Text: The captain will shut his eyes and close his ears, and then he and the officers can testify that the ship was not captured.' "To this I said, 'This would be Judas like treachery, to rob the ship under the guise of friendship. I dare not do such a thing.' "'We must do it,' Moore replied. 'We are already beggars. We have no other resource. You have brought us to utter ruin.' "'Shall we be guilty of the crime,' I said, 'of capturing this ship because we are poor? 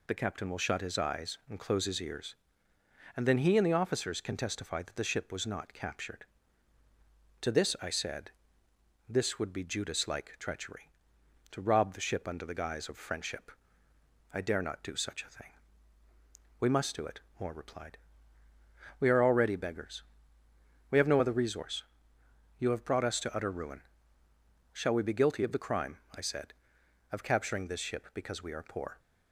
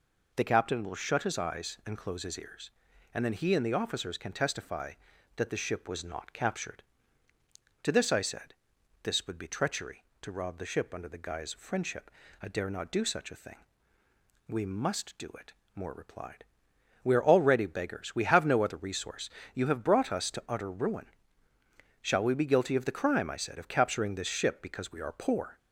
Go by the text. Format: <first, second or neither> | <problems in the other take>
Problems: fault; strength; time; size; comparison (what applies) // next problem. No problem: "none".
first | skips "Judas like"; at 9.4 s